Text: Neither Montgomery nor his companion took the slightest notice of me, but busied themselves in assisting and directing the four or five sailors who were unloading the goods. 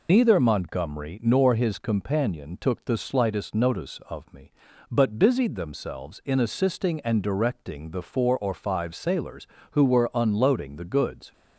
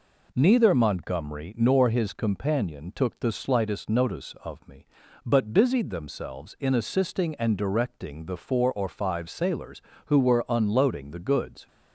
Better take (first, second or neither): second